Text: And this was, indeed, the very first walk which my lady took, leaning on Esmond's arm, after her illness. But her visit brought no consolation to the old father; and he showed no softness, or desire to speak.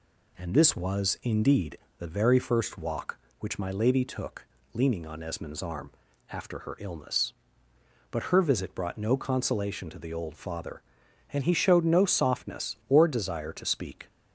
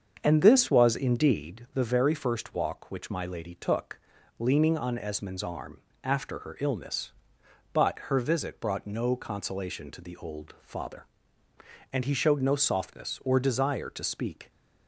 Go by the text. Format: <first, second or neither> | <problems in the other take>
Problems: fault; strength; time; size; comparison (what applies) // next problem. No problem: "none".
first | starts louder than the rest; until 1.7 s; 7 dB